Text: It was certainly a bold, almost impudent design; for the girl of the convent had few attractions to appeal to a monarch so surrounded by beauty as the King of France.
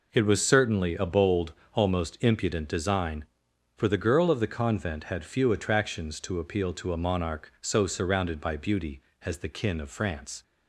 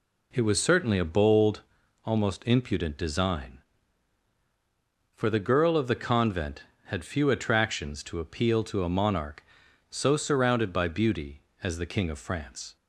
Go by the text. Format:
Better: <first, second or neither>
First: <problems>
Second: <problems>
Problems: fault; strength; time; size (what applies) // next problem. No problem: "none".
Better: second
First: says "Kin" for "King"; at 9.4 s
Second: none